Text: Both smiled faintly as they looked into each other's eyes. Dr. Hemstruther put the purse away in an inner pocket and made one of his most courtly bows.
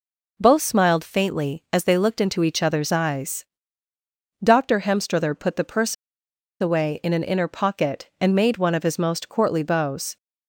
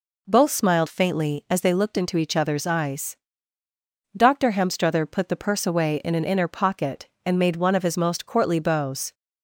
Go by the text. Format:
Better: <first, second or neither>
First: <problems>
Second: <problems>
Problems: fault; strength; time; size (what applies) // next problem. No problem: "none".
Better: second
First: pauses between "purse" and "away"; noticeable; at 5.9 s; 0.65 s long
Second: none